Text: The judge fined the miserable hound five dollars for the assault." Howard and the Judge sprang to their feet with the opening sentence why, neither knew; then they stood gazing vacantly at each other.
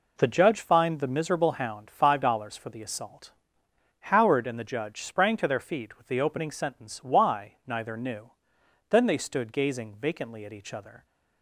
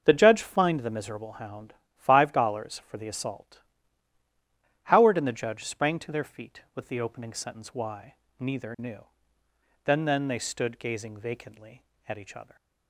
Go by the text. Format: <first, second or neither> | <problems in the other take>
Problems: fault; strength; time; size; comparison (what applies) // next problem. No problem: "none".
first | starts louder than the rest; until 1.0 s; 6.5 dB // pauses between "hound" and "five"; slight; at 1.7 s; 0.24 s long // says "then" twice; at 10.0 s